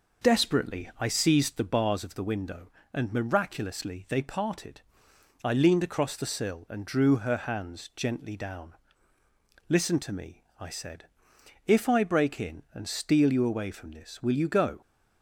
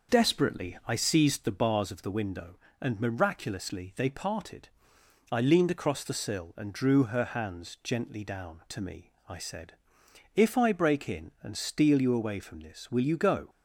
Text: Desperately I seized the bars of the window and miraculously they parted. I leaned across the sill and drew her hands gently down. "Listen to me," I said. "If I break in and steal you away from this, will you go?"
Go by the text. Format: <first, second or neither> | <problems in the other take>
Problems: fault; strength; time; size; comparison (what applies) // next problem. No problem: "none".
first | skips "Listen"; at 8.6 s